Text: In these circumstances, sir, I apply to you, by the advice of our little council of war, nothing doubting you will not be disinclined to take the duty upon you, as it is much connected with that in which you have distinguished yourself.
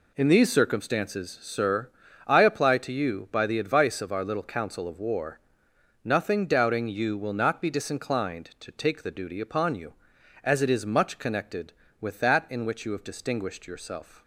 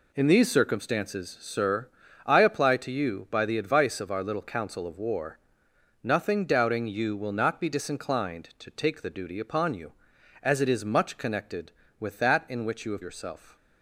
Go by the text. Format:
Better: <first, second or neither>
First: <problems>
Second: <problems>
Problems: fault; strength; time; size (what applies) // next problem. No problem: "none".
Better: first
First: none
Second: skips "distinguished"; at 13.0 s